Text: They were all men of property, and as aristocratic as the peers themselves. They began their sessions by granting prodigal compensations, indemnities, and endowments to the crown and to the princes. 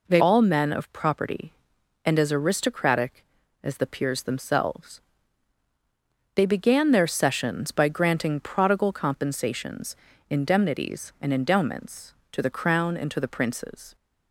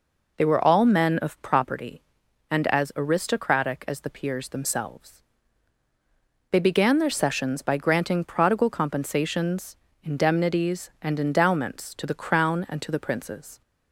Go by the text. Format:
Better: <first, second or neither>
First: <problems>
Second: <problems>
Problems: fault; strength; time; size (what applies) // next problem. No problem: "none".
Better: second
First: skips "were"; at 0.2 s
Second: none